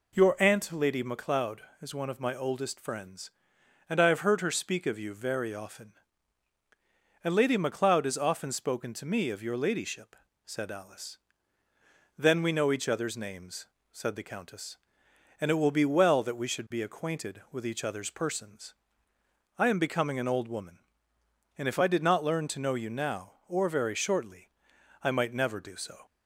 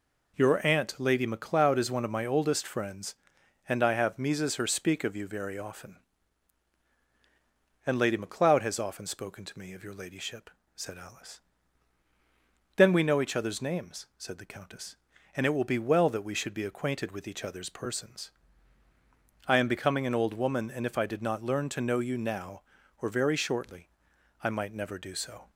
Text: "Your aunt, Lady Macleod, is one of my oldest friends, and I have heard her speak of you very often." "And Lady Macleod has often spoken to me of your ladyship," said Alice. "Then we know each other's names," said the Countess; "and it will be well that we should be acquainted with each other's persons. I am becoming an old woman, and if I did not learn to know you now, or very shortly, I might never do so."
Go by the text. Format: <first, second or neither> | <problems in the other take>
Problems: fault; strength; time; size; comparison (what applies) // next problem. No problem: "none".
first | says "mises" for "heard"; at 4.1 s